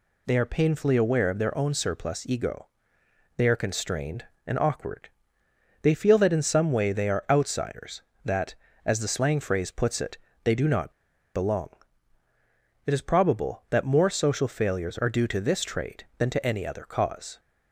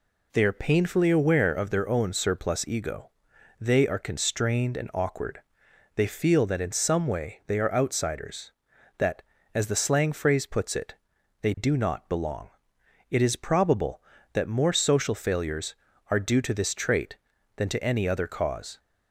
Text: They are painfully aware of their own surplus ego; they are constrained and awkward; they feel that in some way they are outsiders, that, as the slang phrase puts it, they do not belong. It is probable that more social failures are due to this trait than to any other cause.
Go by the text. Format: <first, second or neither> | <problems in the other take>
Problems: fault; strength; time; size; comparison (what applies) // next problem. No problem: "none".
second | pauses between "not" and "belong"; at 10.9 s; 0.44 s long